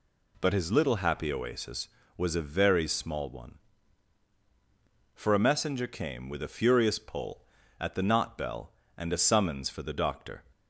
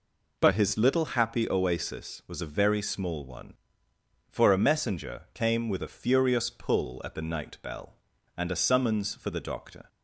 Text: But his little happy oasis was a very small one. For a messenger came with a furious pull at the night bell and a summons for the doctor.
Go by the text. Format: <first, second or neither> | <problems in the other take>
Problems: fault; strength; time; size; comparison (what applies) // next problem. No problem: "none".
second | says "knot" for "night"; at 8.0 s